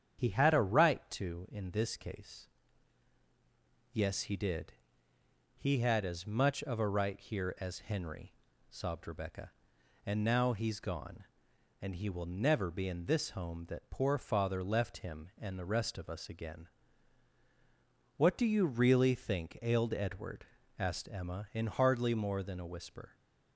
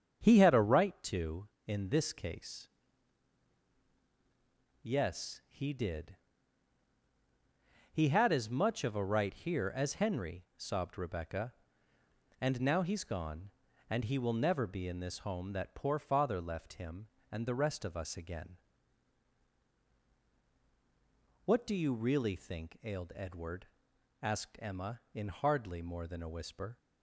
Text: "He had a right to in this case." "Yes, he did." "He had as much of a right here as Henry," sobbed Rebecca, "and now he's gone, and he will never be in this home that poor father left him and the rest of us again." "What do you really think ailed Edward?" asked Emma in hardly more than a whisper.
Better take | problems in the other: neither | starts louder than the rest; strong; the same in both

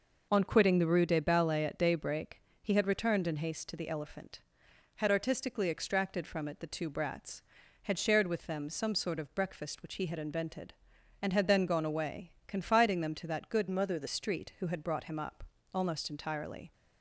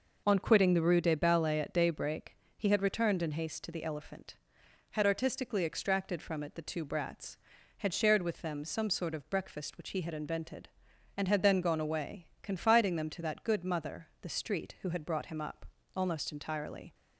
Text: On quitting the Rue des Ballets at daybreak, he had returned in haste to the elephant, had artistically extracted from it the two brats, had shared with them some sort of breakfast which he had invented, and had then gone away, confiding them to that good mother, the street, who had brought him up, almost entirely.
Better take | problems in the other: second | changes voice from "mother" to "the"; from 13.6 to 14.0 s; 0.4 s long

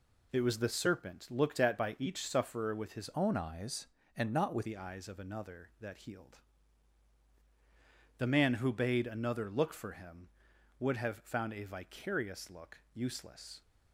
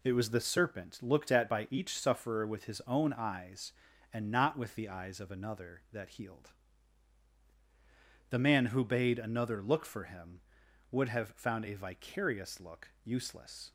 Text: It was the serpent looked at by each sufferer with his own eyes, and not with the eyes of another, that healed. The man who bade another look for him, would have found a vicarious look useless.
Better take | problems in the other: second | changes voice from "own" to "with"; from 3.1 to 4.6 s; 1.5 s long

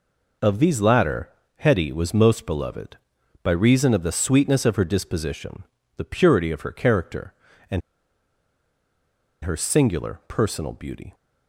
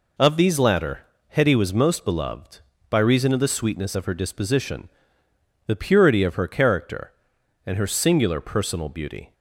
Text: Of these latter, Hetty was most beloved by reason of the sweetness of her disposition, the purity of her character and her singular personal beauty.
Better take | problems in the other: second | pauses between "and" and "her"; strong; at 7.8 s; 1.6 s long

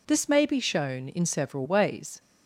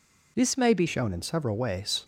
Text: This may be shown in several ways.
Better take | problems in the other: first | changes voice at "shown"; from 0.8 s on; 1.2 s long

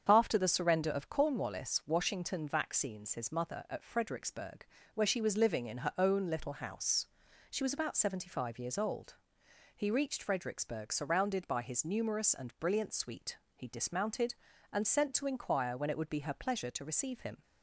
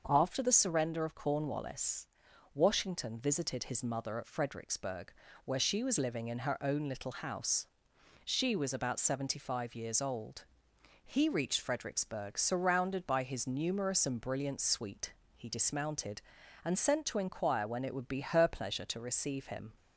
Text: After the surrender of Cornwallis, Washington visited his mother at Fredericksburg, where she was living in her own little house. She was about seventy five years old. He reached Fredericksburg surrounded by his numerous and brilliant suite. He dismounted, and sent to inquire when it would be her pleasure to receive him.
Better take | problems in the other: second | starts louder than the rest; strong; until 1.1 s; 7 dB; also in the second // says "vaccines" for "visited"; at 2.4 s

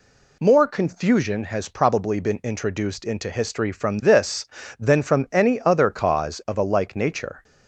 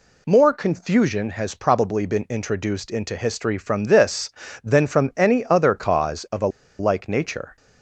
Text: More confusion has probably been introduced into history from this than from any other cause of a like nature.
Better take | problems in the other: first | pauses between "a" and "like"; slight; at 6.4 s; 0.31 s long

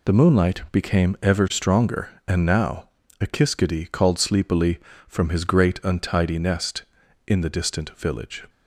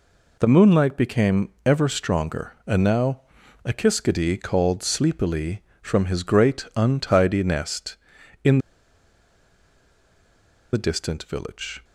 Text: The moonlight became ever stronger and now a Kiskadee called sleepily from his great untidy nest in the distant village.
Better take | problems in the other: first | pauses between "became" and "ever"; slight; at 1.4 s; 0.16 s long // pauses between "now" and "a"; at 3.2 s; 0.44 s long; slight in the first // pauses between "in" and "the"; strong; at 8.5 s; 2.1 s long

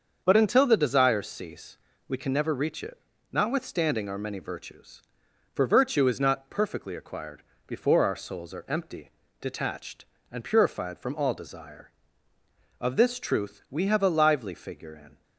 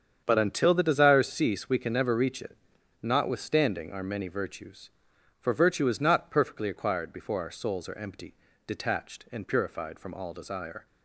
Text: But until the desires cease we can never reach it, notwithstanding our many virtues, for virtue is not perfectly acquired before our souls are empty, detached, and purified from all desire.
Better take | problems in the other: second | starts louder than the rest; until 1.2 s; 7 dB; strong in the second // pauses between "cease" and "we"; slight; at 1.7 s; 0.32 s long // pauses between "acquired" and "before"; slight; at 7.4 s; 0.24 s long // goes on to say "Of this truth we have a lively figure in"; strong; from 12.8 s on; 2.4 s long

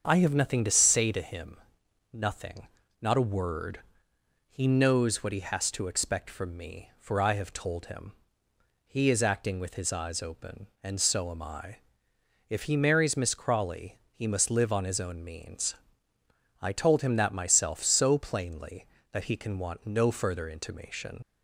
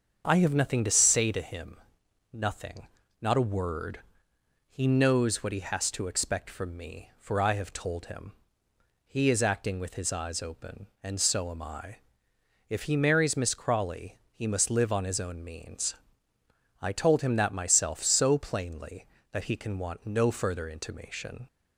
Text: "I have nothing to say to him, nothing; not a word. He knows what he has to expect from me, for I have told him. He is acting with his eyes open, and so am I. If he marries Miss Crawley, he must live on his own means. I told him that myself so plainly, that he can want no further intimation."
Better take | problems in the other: second | starts louder than the rest; until 1.0 s; 7 dB; also in the second // leaves "intimation" unfinished; at 21.2 s; 40 ms

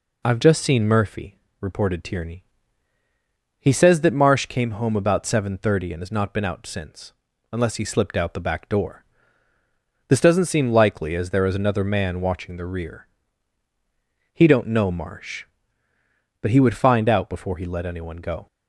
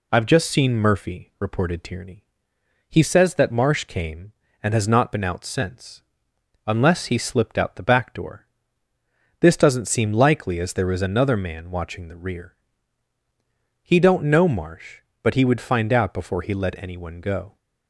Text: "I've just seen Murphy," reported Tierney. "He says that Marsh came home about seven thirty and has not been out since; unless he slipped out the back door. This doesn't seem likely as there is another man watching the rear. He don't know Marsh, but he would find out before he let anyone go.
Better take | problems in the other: first | skips "home about seven thirty"; at 4.4 s

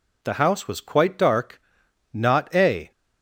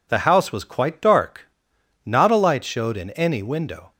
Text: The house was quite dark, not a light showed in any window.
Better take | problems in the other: second | stops before "light showed in any window"; at 2.9 s

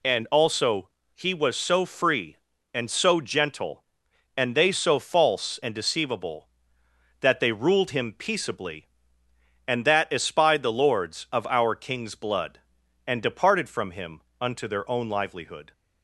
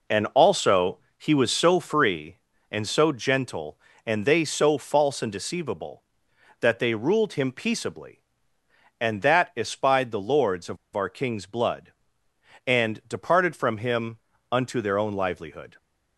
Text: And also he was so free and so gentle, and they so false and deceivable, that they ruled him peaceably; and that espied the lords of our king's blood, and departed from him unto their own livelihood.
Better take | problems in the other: first | pauses between "also" and "he"; slight; at 0.9 s; 0.20 s long; slight in the first // pauses between "of" and "our"; slight; at 10.7 s; 0.18 s long // pauses between "him" and "unto"; slight; at 14.1 s; 0.34 s long; slight in the first

